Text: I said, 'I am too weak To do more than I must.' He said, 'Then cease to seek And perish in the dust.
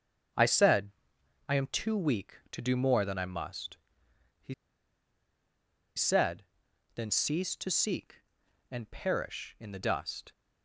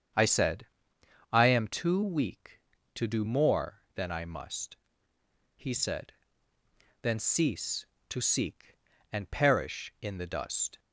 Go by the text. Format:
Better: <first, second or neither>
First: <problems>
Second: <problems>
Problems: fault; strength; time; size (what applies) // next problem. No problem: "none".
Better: second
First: starts louder than the rest; until 1.9 s; 6.5 dB // pauses between "He" and "said"; strong; at 4.5 s; 1.4 s long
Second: starts louder than the rest; strong; until 1.8 s; 7.5 dB